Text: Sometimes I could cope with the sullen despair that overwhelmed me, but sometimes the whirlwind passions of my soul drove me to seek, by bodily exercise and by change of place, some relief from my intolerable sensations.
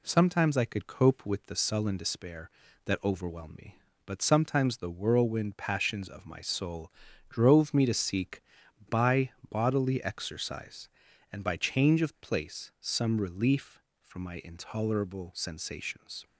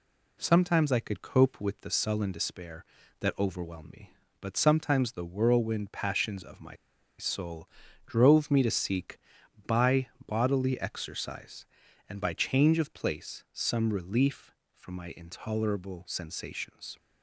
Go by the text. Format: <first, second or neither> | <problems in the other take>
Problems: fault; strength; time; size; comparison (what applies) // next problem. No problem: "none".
first | pauses between "my" and "soul"; at 6.7 s; 0.42 s long // pauses between "soul" and "drove"; at 7.6 s; 0.38 s long; also in the first // pauses between "by" and "bodily"; slight; at 10.0 s; 0.18 s long; slight in the first